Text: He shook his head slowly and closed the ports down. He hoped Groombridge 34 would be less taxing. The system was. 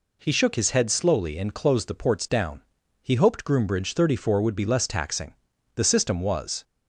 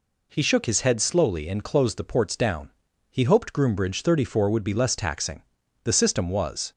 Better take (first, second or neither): neither